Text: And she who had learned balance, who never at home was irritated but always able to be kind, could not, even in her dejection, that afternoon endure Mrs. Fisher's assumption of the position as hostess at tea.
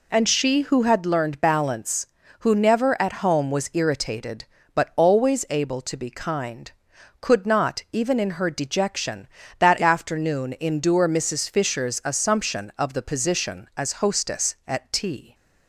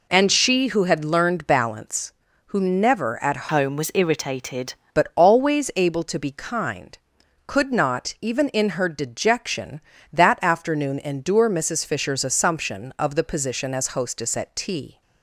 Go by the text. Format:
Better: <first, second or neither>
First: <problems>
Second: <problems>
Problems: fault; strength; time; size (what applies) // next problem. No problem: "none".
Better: first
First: none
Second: changes voice from "home" to "irritated"; from 3.5 to 4.7 s; 1.2 s long